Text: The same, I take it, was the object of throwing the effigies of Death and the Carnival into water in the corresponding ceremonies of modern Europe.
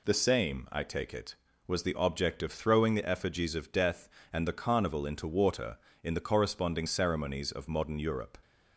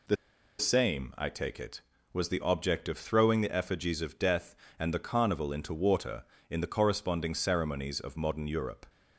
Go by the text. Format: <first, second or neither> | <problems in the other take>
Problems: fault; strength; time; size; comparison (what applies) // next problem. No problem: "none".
first | pauses between "The" and "same"; at 0.1 s; 0.43 s long